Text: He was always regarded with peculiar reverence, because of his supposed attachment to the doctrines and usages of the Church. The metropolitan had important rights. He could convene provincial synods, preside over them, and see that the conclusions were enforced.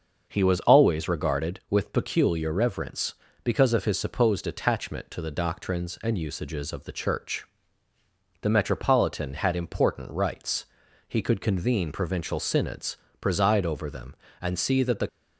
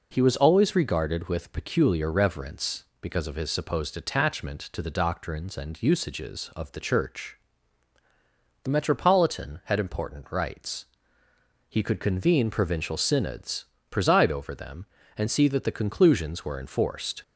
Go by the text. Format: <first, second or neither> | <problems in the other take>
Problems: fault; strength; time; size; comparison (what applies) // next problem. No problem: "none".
second | starts louder than the rest; until 1.2 s; 6 dB // stops before "conclusions were enforced"; at 15.0 s